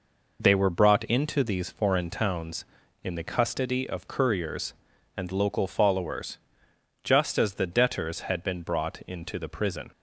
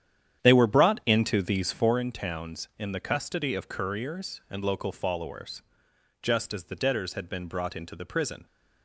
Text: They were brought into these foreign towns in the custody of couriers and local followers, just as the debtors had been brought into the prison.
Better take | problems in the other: first | starts louder than the rest; strong; until 2.1 s; 9.5 dB

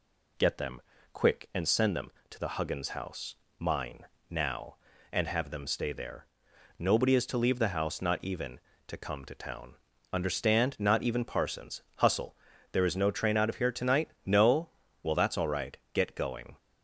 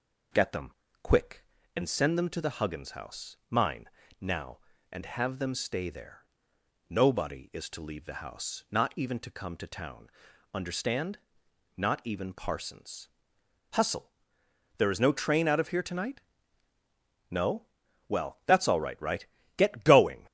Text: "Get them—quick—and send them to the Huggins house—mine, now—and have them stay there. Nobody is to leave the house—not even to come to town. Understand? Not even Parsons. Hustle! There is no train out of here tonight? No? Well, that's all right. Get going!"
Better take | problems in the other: first | says "right" twice; at 18.9 s

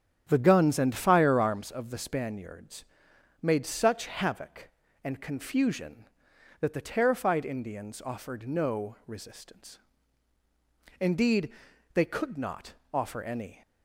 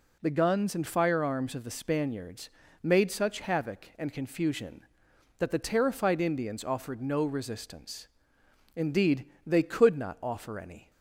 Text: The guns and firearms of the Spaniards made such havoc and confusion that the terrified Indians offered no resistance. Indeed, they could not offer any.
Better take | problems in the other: second | starts louder than the rest; strong; until 1.6 s; 8.5 dB // pauses between "Spaniards" and "made"; noticeable; at 2.8 s; 0.58 s long; slight in the second // pauses between "not" and "offer"; slight; at 12.7 s; 0.18 s long

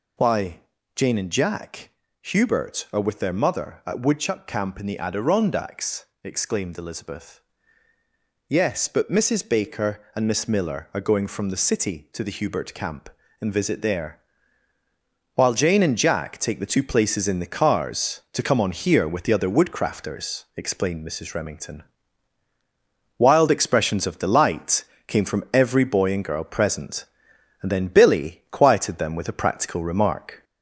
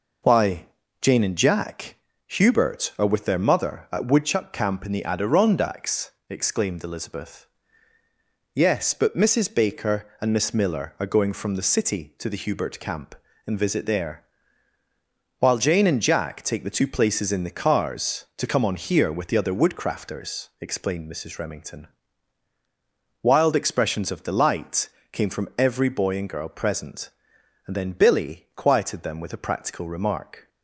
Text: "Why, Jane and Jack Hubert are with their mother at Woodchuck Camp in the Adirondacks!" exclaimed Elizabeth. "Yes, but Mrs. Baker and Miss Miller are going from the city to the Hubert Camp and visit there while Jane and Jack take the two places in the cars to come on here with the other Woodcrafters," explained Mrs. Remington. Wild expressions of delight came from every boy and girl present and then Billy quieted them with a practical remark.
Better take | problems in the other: second | gets louder; slight; throughout; 2.5 dB // pauses between "Jack" and "Hubert"; slight; at 1.9 s; 0.32 s long; slight in the second // pauses between "there" and "while"; at 14.1 s; 1.1 s long; also in the second // pauses between "delight" and "came"; slight; at 24.8 s; 0.22 s long; slight in the second

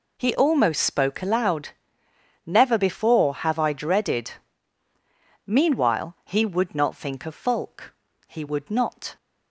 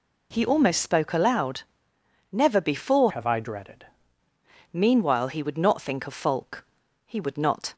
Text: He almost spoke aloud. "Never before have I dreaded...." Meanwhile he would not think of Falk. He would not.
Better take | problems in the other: first | changes voice from "have" to "dreaded"; from 3.0 to 3.8 s; 0.8 s long

